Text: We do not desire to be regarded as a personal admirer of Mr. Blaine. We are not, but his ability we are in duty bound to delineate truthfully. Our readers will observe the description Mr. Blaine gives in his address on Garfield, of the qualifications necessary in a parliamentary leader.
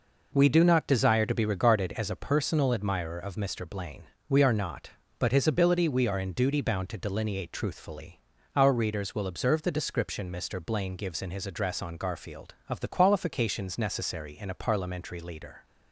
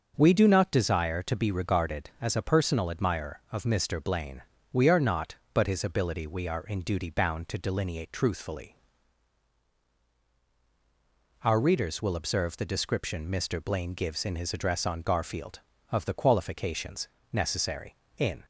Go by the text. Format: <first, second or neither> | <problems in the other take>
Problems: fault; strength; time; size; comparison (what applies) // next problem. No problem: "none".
first | starts louder than the rest; noticeable; until 1.1 s; 6 dB // pauses between "qualifications" and "necessary"; slight; at 17.0 s; 0.24 s long // stops before "a parliamentary leader"; at 18.4 s